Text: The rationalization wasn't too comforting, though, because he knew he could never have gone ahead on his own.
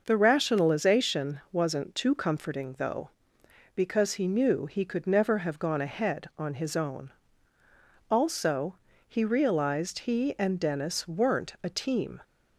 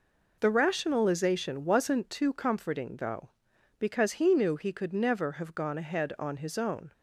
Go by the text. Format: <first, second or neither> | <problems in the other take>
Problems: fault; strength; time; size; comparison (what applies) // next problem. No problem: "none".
second | goes on to say "Also he realized he and Dennis weren't a team"; strong; from 8.0 s on; 4.1 s long